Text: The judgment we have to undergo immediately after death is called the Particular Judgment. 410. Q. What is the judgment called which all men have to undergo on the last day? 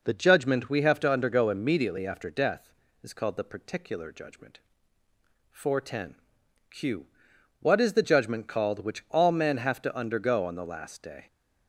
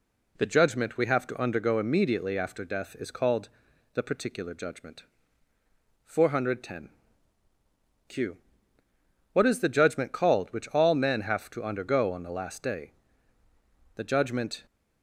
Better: first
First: none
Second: pauses between "called" and "the"; noticeable; at 3.4 s; 0.46 s long // goes on to say "The judgment"; noticeable; from 13.9 s on; 0.70 s long

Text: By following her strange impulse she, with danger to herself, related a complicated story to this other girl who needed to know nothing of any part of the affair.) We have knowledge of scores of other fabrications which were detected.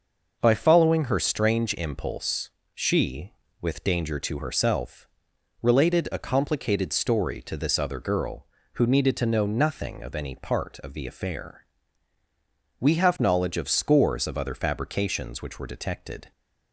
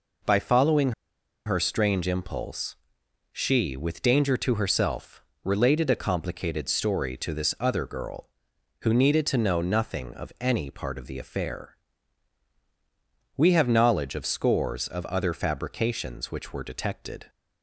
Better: first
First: pauses between "impulse" and "she"; slight; at 2.4 s; 0.22 s long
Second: pauses between "following" and "her"; noticeable; at 0.9 s; 0.54 s long // pauses between "impulse" and "she"; noticeable; at 2.7 s; 0.56 s long

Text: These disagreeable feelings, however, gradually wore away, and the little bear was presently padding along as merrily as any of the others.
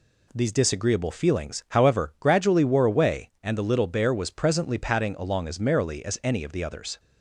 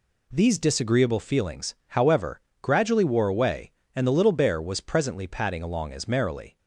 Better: first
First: none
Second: stops before "as any of the others"; at 6.5 s

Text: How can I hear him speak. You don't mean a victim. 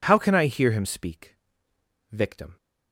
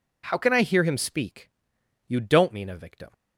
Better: second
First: skips "You don't mean a"; at 1.7 s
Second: none

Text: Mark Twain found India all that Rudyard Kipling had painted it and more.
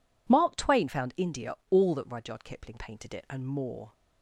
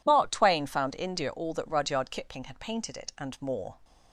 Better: second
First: pauses between "India" and "all"; slight; at 1.5 s; 0.16 s long // skips "had"; at 2.7 s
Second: none

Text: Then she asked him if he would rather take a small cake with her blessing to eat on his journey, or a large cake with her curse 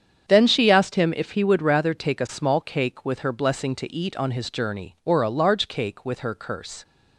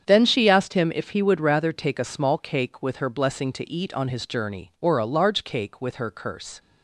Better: neither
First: starts louder than the rest; strong; until 1.3 s; 8 dB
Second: starts louder than the rest; strong; until 1.0 s; 8 dB

